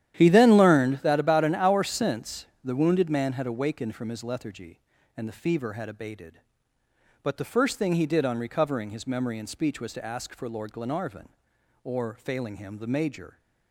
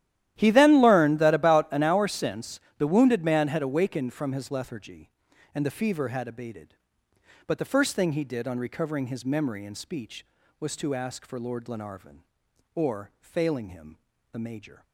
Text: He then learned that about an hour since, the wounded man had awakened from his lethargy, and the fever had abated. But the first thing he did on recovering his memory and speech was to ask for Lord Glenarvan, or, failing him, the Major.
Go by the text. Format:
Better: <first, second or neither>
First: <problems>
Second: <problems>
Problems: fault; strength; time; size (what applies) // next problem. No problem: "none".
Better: neither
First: starts louder than the rest; strong; until 1.2 s; 11 dB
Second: starts louder than the rest; strong; until 1.3 s; 12.5 dB